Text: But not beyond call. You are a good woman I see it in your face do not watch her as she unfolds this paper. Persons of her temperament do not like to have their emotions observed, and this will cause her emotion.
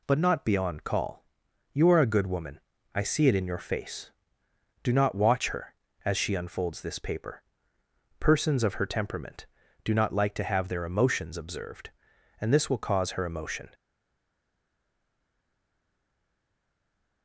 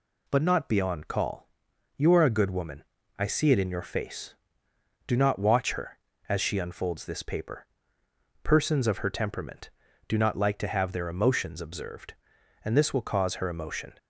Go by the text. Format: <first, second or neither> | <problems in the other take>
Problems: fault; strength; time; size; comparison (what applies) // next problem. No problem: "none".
second | pauses between "woman" and "I"; slight; at 2.5 s; 0.34 s long; slight in the second // stays silent after the last word; strong; from 13.7 s on; 3.5 s long